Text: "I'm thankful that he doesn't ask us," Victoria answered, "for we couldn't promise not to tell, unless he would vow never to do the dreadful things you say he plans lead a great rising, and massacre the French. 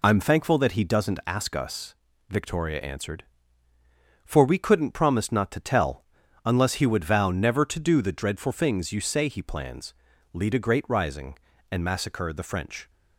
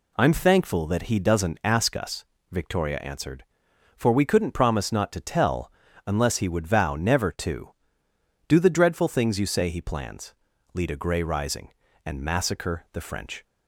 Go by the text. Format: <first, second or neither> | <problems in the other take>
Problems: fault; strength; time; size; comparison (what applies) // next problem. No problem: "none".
first | pauses between "plans" and "lead"; at 10.3 s; 0.40 s long; also in the first // says "grey" for "great"; at 10.9 s